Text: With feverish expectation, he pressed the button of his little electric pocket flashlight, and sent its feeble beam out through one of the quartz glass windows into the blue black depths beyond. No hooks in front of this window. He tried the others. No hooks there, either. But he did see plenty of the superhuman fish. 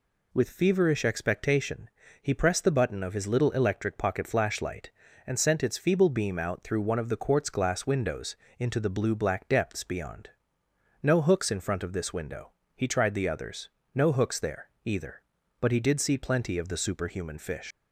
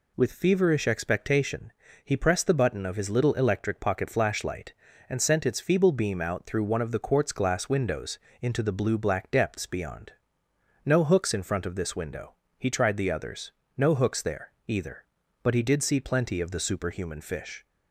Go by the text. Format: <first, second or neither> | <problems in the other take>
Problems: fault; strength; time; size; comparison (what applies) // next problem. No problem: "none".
second | pauses between "windows" and "into"; slight; at 8.3 s; 0.22 s long; slight in the second // leaves "fish" unfinished; at 17.7 s; 125 ms